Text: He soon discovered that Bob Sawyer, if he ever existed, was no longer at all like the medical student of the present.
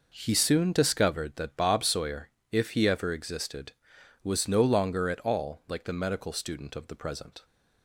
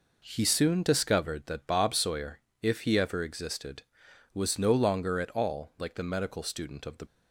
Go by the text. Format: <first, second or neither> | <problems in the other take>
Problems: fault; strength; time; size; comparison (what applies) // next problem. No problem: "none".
first | stops before "present"; at 7.0 s